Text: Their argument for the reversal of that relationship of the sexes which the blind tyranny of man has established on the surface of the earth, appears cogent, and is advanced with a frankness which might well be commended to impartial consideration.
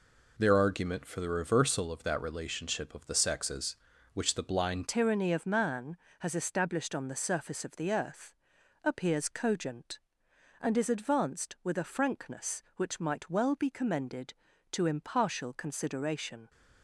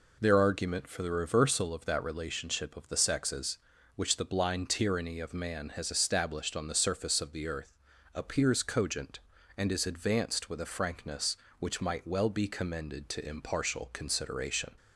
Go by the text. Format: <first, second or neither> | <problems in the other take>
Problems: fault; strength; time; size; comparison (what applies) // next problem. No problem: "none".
second | changes voice at "tyranny"; from 4.8 s on; 11.6 s long